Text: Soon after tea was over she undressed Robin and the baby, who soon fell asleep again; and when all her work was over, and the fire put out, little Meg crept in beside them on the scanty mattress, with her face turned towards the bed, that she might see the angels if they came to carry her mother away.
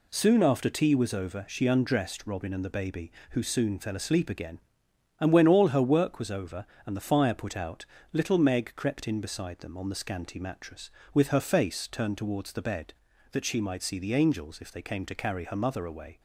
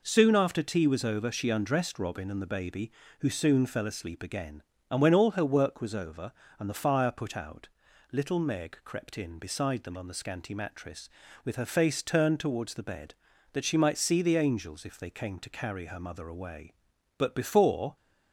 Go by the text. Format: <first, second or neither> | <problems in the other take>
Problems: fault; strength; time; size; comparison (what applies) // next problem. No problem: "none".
first | goes on to say "But before"; noticeable; from 17.1 s on; 0.76 s long